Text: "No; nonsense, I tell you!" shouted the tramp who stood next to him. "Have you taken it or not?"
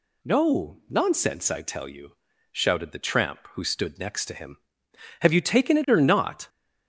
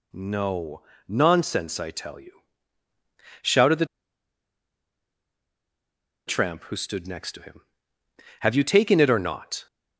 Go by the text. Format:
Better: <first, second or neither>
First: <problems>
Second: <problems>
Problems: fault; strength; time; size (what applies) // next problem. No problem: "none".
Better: first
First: none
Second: pauses between "the" and "tramp"; strong; at 3.8 s; 2.4 s long